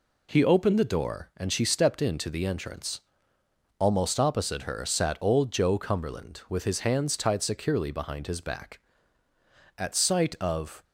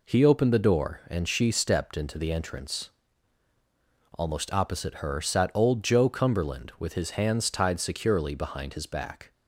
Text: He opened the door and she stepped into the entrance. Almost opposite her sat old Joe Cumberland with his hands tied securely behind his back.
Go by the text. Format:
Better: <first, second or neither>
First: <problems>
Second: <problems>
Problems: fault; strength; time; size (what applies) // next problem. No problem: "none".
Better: second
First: goes on to say "At sight of"; noticeable; from 9.7 s on; 1.0 s long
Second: none